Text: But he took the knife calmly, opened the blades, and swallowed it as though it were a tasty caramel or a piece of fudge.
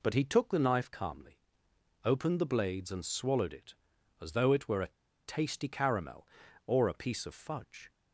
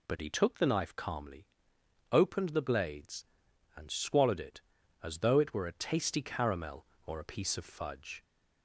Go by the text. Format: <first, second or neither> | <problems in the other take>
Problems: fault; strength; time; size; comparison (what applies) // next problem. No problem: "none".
second | pauses between "a" and "tasty"; at 4.8 s; 0.37 s long